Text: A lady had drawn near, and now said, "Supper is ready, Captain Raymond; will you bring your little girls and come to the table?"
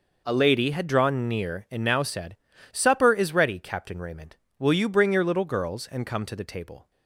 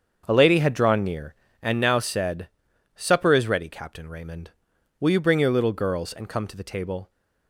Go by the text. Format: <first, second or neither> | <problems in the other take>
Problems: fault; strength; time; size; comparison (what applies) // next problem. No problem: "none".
first | starts louder than the rest; until 1.8 s; 7 dB